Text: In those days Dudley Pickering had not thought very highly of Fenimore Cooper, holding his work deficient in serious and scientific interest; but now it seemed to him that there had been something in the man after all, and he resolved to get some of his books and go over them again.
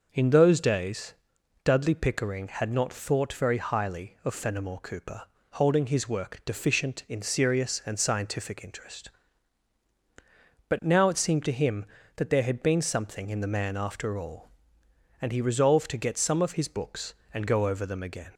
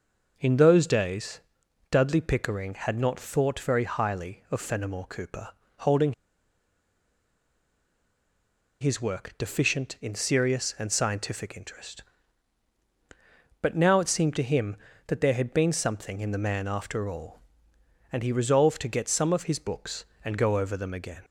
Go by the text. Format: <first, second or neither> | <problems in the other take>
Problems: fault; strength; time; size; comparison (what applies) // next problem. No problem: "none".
first | pauses between "days" and "Dudley"; noticeable; at 1.4 s; 0.50 s long; noticeable in the first // pauses between "holding" and "his"; strong; at 6.1 s; 2.6 s long